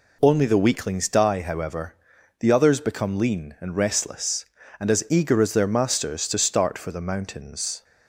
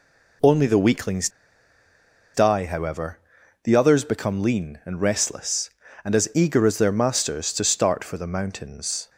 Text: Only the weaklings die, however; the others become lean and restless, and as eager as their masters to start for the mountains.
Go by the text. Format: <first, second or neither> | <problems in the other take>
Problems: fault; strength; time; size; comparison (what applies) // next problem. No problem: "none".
first | pauses between "weaklings" and "die"; at 1.2 s; 1.0 s long